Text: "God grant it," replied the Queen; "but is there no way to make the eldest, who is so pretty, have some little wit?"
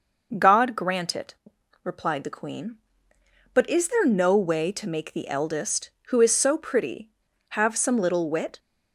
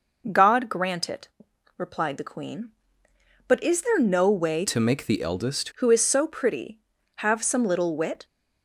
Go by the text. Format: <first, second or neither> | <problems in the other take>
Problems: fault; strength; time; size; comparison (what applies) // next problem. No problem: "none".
first | changes voice from "to" to "eldest"; from 4.6 to 5.6 s; 1.0 s long